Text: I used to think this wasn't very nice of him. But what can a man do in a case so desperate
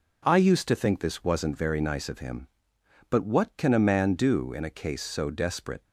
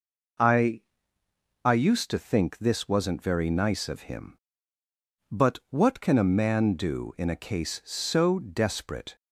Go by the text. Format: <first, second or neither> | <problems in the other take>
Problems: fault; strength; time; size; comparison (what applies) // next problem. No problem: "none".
first | says "I" twice; at 1.6 s